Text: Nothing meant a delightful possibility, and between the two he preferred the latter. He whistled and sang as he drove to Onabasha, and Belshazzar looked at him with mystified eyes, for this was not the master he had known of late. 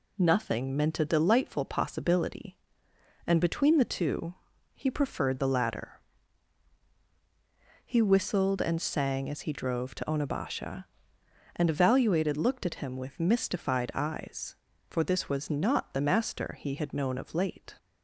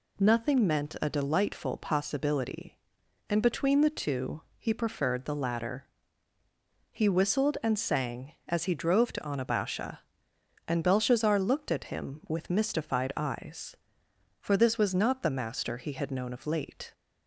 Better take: second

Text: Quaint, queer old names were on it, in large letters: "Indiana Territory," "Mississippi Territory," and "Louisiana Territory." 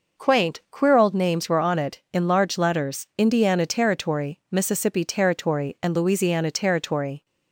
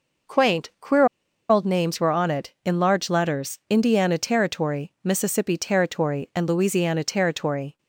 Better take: first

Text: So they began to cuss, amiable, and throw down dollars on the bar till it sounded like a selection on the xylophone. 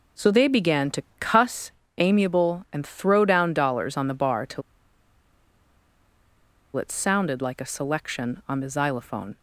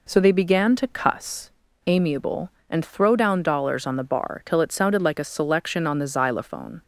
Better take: second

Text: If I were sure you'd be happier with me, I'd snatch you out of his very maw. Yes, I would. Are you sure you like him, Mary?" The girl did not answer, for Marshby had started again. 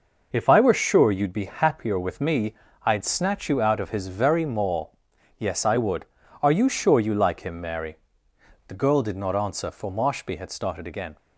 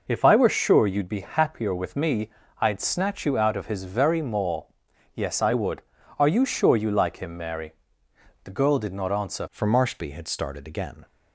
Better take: first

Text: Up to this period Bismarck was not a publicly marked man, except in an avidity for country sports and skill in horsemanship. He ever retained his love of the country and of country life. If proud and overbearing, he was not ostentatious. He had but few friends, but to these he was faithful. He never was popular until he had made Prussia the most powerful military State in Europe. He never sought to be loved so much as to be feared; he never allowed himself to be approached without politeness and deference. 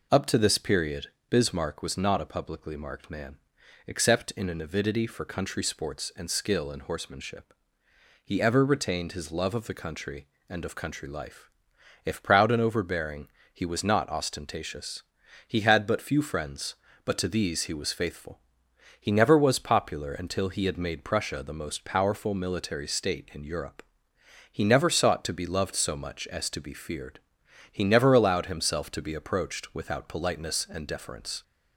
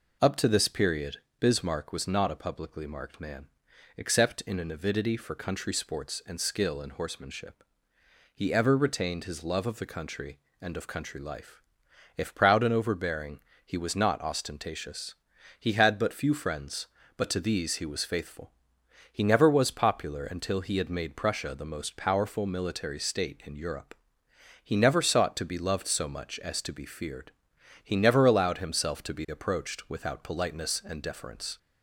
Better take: neither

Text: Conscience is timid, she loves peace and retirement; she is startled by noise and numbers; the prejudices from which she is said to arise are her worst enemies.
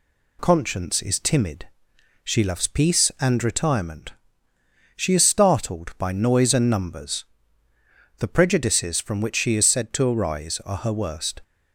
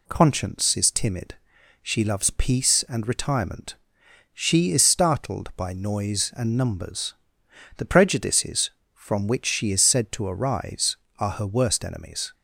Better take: second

